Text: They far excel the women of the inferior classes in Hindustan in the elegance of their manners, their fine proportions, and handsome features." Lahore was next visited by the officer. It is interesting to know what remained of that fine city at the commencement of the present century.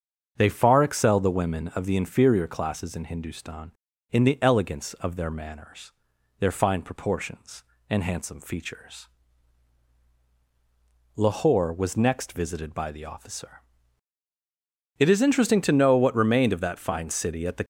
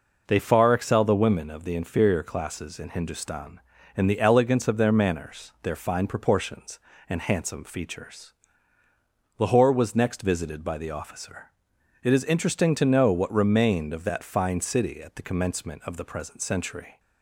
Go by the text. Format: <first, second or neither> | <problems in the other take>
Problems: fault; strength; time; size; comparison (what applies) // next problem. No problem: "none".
second | starts louder than the rest; until 1.3 s; 7 dB // stops before "commencement of the present century"; at 17.6 s